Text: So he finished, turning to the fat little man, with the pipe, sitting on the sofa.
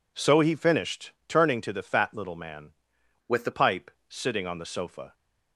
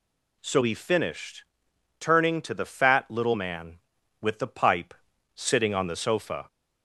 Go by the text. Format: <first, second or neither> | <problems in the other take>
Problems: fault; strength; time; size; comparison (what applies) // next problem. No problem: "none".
second | changes voice from "with" to "the"; from 3.2 to 3.5 s; 0.3 s long